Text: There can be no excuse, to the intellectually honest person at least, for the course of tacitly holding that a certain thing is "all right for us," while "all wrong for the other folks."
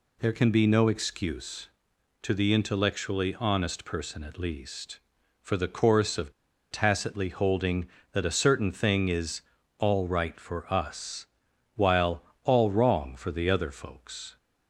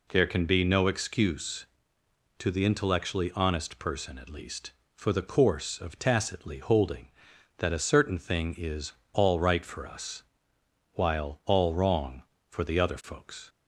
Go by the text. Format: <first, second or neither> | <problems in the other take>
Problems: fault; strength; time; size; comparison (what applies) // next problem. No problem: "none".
second | pauses between "of" and "tacitly"; at 6.3 s; 0.38 s long // pauses between "is" and "all"; slight; at 9.4 s; 0.34 s long; slight in the second // pauses between "while" and "all"; slight; at 12.2 s; 0.18 s long